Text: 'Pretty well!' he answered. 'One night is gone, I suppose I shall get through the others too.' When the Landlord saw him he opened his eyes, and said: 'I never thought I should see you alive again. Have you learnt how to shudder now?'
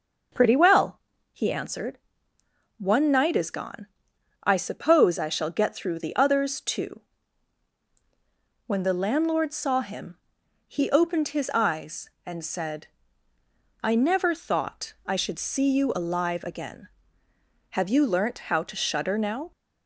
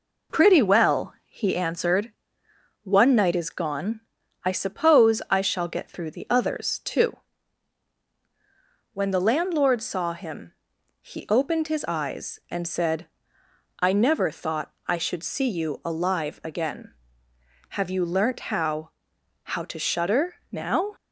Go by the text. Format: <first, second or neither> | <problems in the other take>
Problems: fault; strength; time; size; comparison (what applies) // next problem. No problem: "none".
first | pauses between "him" and "he"; noticeable; at 10.5 s; 0.50 s long; noticeable in the first // pauses between "thought" and "I"; slight; at 14.7 s; 0.16 s long // says "how" twice; at 19.4 s